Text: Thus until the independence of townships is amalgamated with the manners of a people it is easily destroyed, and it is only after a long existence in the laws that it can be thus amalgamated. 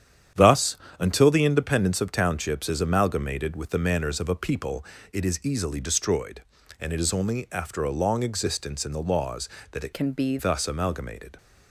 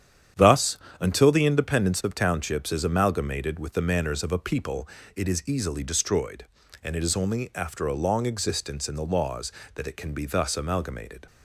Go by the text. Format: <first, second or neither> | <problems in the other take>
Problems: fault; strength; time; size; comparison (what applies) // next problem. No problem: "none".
second | starts louder than the rest; strong; until 1.5 s; 9 dB; strong in the second // pauses between "Thus" and "until"; slight; at 0.7 s; 0.22 s long; slight in the second // pauses between "people" and "it"; slight; at 4.8 s; 0.26 s long; slight in the second // changes voice from "can" to "be"; from 9.9 to 10.3 s; 0.4 s long